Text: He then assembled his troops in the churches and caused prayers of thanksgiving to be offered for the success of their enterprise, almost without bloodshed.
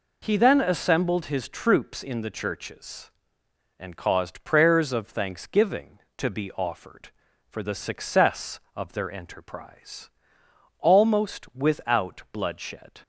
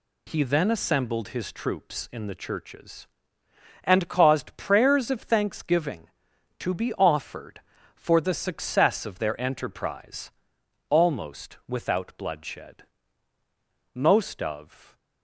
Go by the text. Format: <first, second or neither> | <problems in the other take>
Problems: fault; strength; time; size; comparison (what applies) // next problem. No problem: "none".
first | goes on to say "Most of"; noticeable; from 13.9 s on; 1.0 s long